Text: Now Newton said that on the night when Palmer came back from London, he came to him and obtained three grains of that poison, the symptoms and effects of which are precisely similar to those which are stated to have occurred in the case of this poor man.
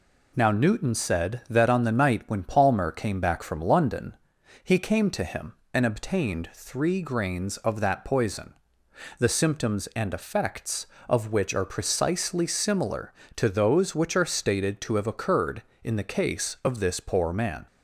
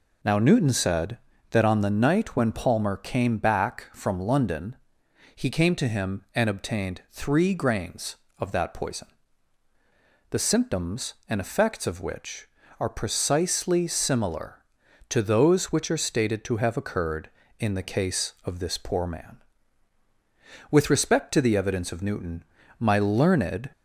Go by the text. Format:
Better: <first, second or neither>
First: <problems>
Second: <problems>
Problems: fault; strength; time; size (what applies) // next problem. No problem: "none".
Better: first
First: none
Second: goes on to say "With respect to the evidence of Newton my learned"; strong; from 20.6 s on; 3.0 s long